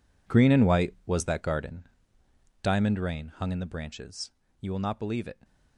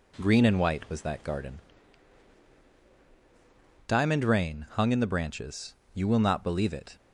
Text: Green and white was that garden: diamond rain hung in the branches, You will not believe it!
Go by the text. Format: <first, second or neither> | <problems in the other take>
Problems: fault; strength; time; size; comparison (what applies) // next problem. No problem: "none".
second | gets quieter; strong; throughout; 15 dB